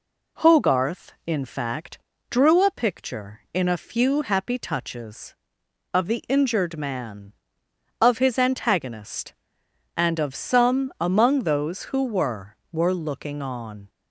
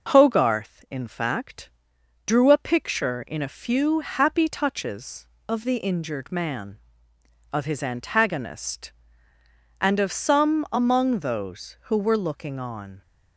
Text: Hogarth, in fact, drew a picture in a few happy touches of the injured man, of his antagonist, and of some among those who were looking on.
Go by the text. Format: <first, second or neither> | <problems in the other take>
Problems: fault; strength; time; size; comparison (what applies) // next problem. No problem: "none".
second | says "were" twice; at 12.7 s